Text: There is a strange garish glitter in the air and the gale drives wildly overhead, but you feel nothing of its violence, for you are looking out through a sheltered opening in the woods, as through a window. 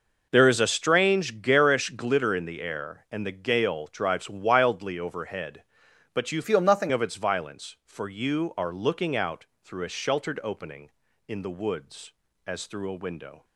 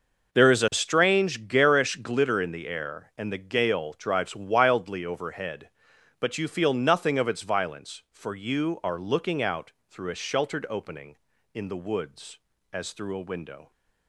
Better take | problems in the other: second | changes voice from "feel" to "nothing"; from 6.4 to 6.9 s; 0.5 s long // pauses between "out" and "through"; slight; at 9.4 s; 0.18 s long; slight in the second

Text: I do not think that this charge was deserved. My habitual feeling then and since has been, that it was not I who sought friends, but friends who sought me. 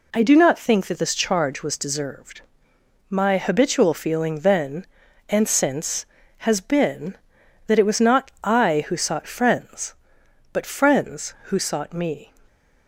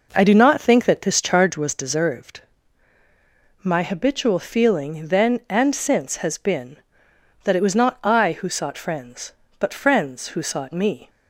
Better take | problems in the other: first | starts louder than the rest; noticeable; until 1.6 s; 5 dB

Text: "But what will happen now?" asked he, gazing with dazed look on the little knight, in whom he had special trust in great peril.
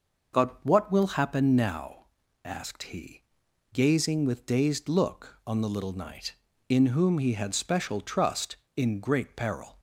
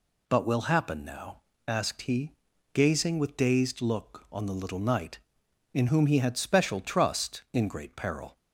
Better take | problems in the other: first | skips "what"; at 0.4 s

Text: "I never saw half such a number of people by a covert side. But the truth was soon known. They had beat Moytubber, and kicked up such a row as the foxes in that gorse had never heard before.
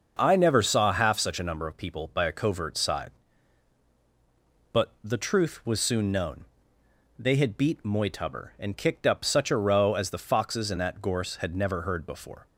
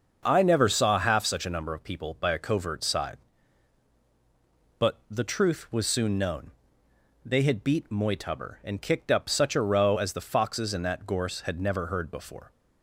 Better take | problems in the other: neither | starts louder than the rest; the same in both

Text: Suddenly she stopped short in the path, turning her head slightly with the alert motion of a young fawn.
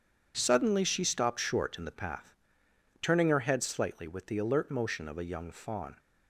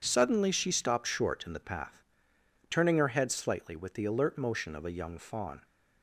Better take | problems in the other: neither | none

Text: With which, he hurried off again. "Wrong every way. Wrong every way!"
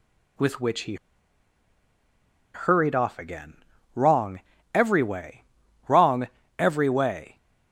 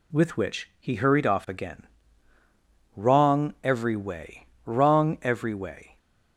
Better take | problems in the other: second | pauses between "he" and "hurried"; strong; at 0.9 s; 1.5 s long // pauses between "Wrong" and "every"; slight; at 4.4 s; 0.32 s long // pauses between "Wrong" and "every"; slight; at 6.2 s; 0.32 s long

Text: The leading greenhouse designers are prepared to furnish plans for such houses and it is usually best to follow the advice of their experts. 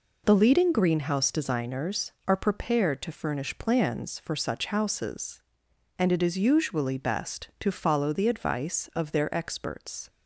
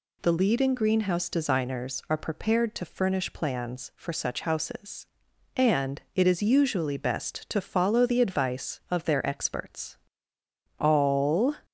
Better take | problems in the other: first | goes on to say "All"; noticeable; from 10.7 s on; 0.76 s long

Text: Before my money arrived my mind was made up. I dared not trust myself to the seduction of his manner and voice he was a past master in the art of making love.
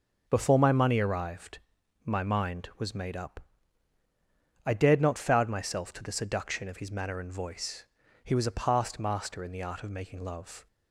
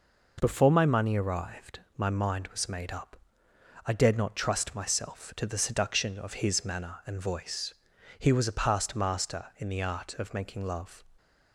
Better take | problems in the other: second | starts louder than the rest; until 1.2 s; 6 dB // pauses between "arrived" and "my"; noticeable; at 1.5 s; 0.50 s long; slight in the second // says "foud" for "trust"; at 5.1 s // pauses between "voice" and "he"; at 7.8 s; 0.40 s long; also in the second

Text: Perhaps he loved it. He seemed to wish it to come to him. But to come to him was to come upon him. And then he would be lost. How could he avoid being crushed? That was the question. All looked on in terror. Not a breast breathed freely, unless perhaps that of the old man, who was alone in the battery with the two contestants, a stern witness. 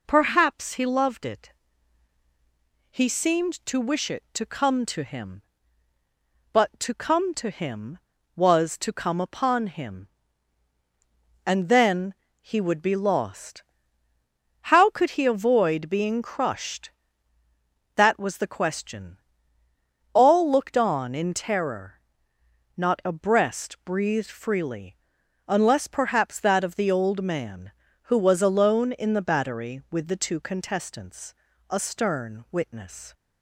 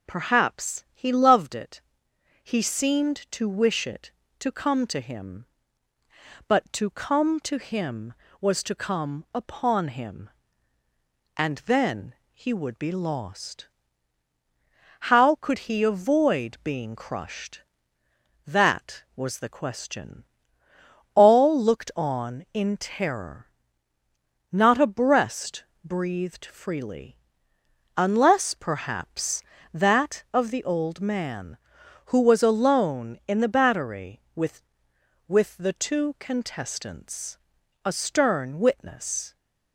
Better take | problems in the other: first | pauses between "then" and "he"; slight; at 12.1 s; 0.18 s long; slight in the first // pauses between "breast" and "breathed"; slight; at 25.6 s; 0.20 s long // says "with" twice; at 35.2 s

